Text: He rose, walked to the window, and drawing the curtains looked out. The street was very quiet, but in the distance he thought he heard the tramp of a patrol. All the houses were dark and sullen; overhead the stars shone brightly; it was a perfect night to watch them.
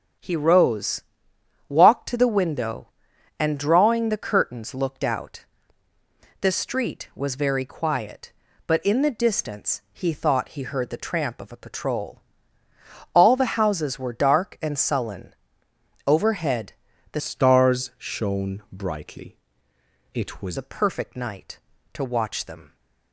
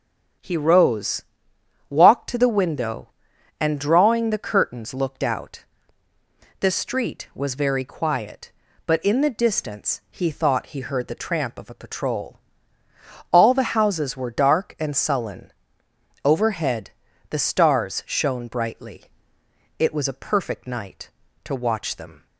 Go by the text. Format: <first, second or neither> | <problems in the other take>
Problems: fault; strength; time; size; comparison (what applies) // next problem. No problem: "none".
second | starts louder than the rest; strong; until 1.8 s; 8 dB; also in the second // pauses between "overhead" and "the"; at 16.7 s; 0.40 s long; also in the second // changes voice from "stars" to "was"; from 17.2 to 20.5 s; 3.3 s long